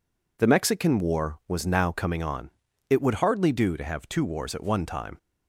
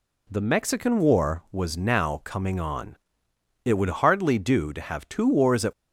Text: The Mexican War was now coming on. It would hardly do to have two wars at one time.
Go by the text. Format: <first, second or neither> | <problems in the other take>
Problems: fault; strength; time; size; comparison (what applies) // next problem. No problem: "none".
first | stops before "one time"; at 5.7 s